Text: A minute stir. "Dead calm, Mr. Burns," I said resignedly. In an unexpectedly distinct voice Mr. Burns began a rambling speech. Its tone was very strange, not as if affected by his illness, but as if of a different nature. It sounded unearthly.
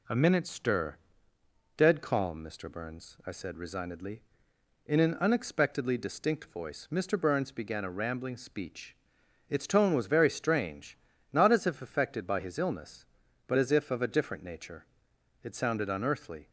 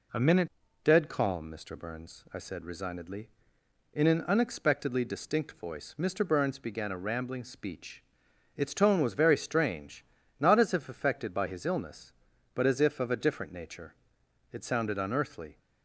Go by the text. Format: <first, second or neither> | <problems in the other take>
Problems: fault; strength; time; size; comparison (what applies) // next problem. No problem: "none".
first | skips "stir"; at 0.6 s